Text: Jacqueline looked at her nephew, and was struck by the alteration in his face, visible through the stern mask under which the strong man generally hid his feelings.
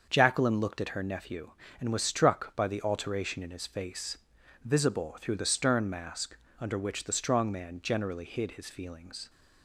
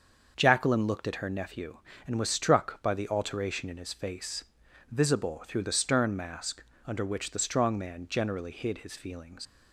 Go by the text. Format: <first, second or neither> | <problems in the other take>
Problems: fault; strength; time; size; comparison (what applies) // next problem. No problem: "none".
first | starts louder than the rest; until 1.3 s; 6.5 dB; also in the first // pauses between "mask" and "under"; slight; at 6.6 s; 0.24 s long; slight in the first // leaves "feelings" unfinished; at 9.4 s; 110 ms